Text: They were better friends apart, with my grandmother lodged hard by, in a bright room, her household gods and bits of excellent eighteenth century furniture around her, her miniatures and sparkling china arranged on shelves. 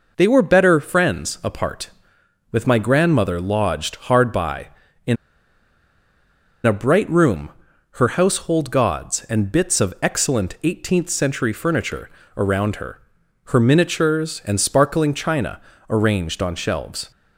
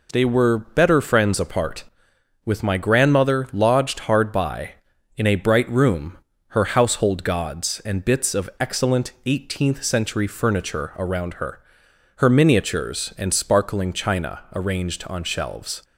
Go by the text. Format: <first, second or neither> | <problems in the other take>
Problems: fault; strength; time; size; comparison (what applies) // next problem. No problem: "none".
second | pauses between "in" and "a"; strong; at 5.1 s; 1.5 s long // pauses between "furniture" and "around"; slight; at 12.0 s; 0.28 s long // pauses between "china" and "arranged"; slight; at 15.6 s; 0.28 s long